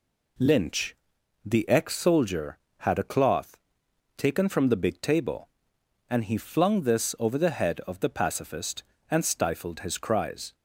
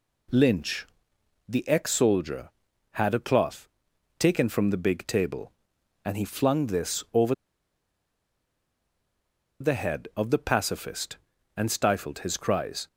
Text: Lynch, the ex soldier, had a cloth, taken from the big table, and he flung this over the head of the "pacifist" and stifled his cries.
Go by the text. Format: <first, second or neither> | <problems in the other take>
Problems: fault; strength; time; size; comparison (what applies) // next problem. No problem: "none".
first | pauses between "over" and "the"; strong; at 7.3 s; 2.2 s long